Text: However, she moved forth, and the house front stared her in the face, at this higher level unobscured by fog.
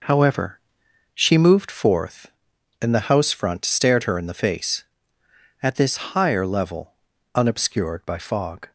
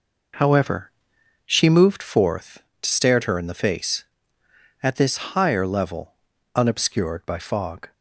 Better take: first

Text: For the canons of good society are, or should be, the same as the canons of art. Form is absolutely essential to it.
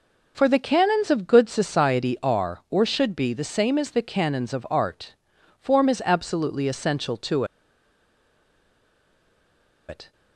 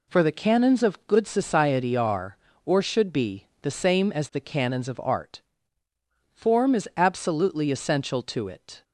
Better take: second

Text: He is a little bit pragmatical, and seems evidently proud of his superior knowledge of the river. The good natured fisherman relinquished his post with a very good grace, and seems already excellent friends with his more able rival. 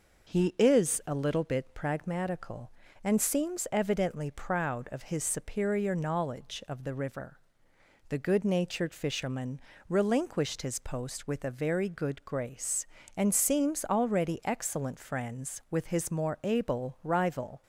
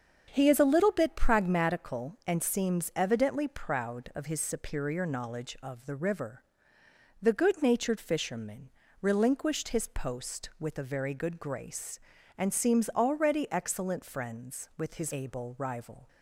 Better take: first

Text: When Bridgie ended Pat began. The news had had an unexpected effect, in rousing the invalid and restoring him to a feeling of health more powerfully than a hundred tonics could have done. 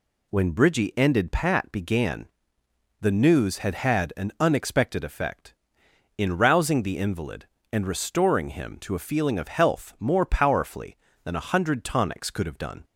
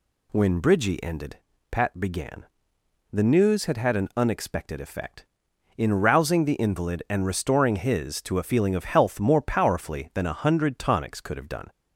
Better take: first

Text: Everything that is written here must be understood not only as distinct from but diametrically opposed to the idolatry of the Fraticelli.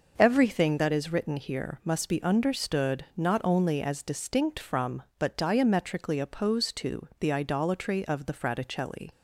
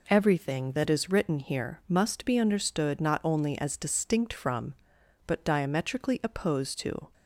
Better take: first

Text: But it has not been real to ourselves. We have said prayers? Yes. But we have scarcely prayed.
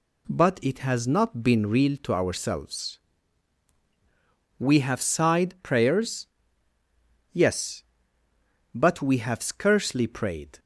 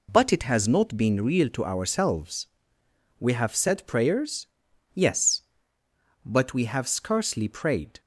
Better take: second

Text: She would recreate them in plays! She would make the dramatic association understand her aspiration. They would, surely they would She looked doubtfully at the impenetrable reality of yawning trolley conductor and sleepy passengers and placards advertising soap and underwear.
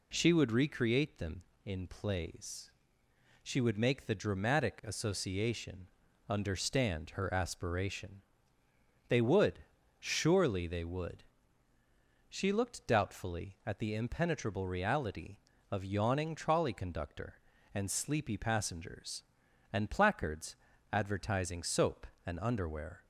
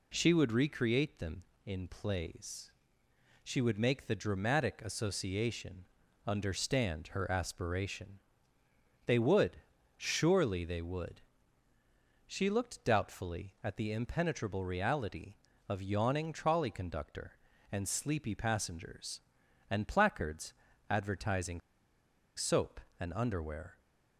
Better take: first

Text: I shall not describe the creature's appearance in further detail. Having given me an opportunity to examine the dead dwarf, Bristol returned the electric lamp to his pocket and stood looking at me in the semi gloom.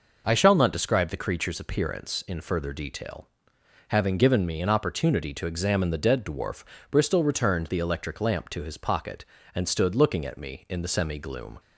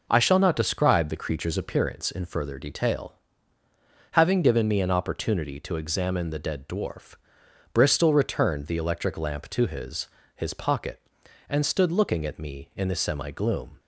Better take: first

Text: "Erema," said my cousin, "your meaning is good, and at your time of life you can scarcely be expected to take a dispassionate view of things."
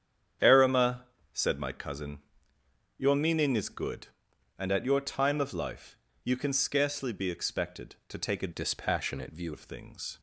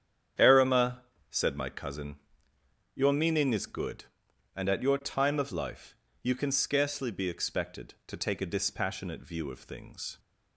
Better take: second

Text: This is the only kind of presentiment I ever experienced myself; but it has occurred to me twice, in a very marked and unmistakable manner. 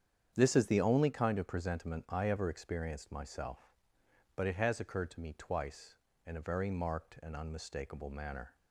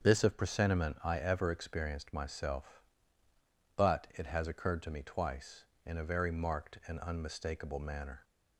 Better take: first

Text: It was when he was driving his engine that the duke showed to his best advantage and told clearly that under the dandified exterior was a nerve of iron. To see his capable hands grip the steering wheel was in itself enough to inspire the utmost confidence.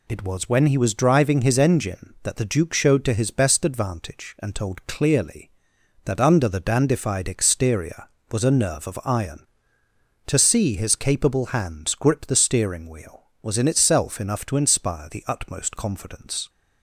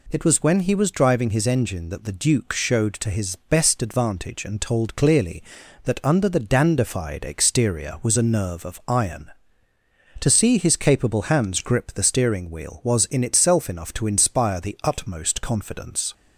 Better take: neither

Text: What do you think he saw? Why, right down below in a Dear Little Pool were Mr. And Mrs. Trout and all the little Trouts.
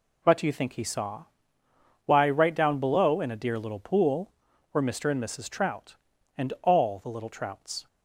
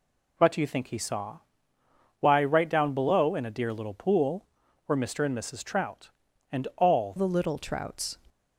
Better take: first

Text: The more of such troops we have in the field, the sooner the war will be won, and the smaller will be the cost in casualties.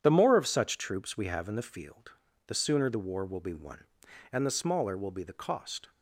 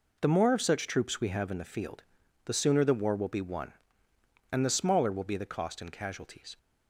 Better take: second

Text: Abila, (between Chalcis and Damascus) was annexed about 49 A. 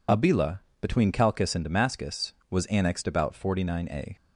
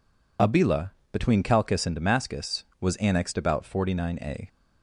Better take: neither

